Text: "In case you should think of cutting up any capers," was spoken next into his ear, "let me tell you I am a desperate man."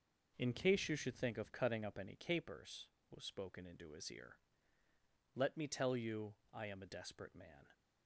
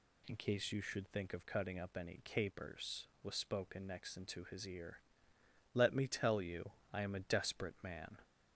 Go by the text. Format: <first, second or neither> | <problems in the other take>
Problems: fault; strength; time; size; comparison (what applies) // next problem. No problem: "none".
second | skips "next"; at 3.6 s // pauses between "you" and "I"; slight; at 6.3 s; 0.18 s long; slight in the second